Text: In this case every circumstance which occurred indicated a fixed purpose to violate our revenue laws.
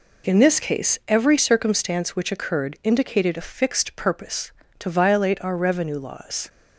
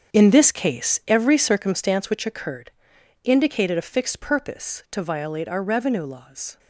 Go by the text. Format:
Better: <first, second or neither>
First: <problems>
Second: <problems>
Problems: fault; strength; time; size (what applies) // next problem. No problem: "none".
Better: first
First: none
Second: gets quieter; strong; throughout; 12 dB // pauses between "occurred" and "indicated"; noticeable; at 2.7 s; 0.54 s long